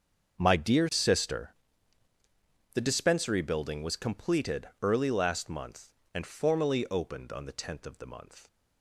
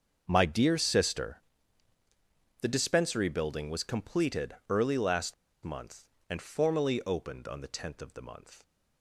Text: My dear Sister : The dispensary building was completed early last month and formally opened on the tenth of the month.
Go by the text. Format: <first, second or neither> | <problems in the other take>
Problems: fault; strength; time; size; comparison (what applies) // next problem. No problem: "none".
first | starts louder than the rest; until 1.2 s; 6.5 dB; also in the first // pauses between "last" and "month"; slight; at 5.3 s; 0.30 s long